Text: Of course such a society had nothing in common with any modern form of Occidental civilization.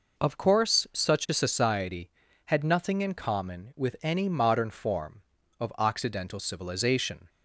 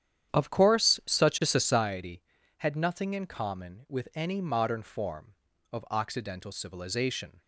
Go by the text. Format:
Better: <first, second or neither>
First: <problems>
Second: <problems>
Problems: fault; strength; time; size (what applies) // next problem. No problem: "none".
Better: first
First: none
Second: starts louder than the rest; strong; until 1.9 s; 9.5 dB